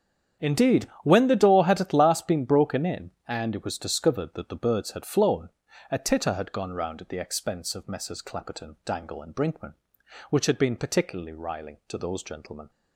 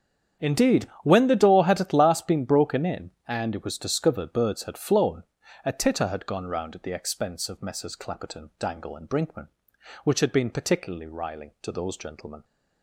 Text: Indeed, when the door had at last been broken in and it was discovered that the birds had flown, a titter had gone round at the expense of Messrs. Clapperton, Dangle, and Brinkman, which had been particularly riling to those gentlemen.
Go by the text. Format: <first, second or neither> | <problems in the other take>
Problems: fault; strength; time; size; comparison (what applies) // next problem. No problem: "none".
first | starts louder than the rest; strong; until 1.5 s; 8 dB; strong in the first // skips "that the"; at 4.3 s